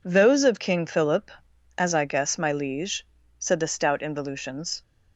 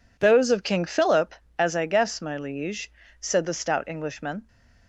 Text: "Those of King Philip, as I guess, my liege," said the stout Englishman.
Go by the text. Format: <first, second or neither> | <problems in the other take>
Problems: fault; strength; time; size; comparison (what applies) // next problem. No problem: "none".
second | says "Involutions" for "Englishman"; at 3.9 s